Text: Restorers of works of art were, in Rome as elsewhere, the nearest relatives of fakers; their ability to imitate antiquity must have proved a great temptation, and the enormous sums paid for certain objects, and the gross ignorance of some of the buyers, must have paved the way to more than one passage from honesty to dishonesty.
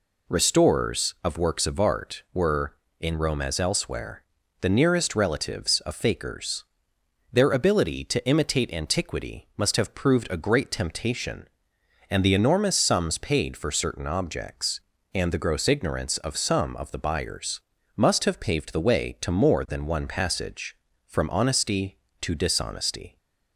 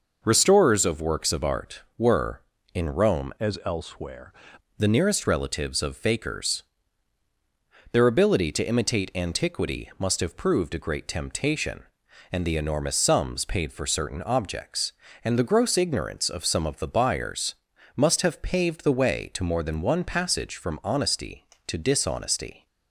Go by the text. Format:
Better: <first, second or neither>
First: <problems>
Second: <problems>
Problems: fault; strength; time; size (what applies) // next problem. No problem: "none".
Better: first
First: none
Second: changes voice from "as" to "elsewhere"; from 3.3 to 4.3 s; 1.0 s long